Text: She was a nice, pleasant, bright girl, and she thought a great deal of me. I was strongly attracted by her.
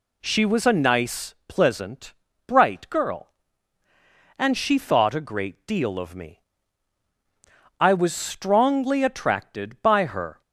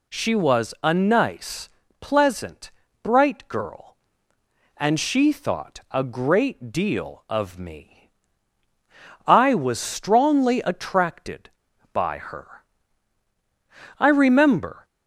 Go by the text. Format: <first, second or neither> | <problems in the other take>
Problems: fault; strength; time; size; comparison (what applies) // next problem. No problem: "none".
first | goes on to say "I remember"; noticeable; from 13.9 s on; 0.86 s long